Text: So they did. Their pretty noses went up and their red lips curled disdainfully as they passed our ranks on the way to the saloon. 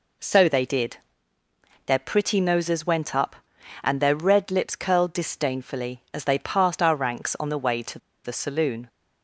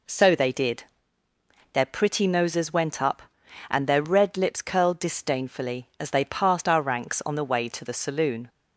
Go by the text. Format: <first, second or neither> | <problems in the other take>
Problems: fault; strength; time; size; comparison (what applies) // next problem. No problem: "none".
second | pauses between "to" and "the"; slight; at 7.9 s; 0.26 s long